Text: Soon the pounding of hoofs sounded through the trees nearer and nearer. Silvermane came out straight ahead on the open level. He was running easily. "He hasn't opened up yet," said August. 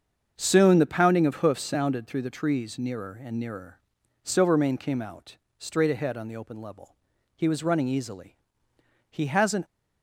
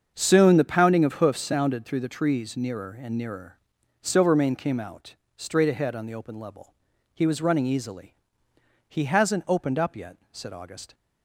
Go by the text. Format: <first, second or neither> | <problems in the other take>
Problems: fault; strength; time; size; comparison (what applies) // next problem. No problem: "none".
second | starts louder than the rest; until 1.3 s; 7 dB; also in the second // pauses between "out" and "straight"; slight; at 5.3 s; 0.20 s long; slight in the second // stops before "opened up yet said August"; at 9.6 s